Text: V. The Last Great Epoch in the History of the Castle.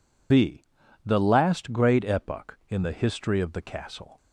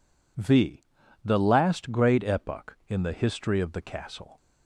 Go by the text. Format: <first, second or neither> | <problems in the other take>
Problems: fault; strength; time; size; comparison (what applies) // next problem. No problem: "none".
second | loses the start of "V"; at 0.3 s; 125 ms